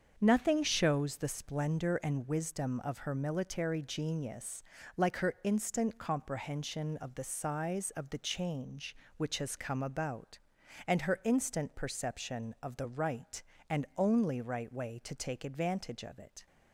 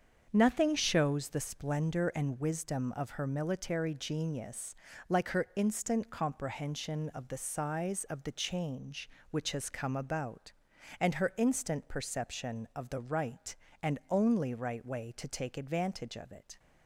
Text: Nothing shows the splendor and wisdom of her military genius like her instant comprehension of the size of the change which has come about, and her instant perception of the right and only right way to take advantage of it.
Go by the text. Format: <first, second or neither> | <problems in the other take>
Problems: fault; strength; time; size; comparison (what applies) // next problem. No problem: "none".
neither | starts louder than the rest; the same in both // pauses between "genius" and "like"; slight; the same in both